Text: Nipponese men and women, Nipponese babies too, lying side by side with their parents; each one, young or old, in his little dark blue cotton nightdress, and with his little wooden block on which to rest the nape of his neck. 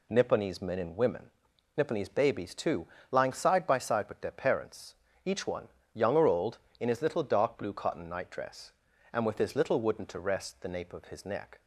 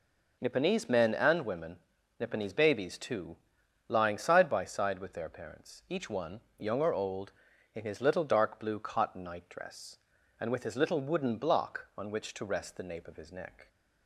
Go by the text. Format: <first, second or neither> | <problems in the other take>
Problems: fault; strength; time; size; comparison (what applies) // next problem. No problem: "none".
second | skips "block on which"; at 10.0 s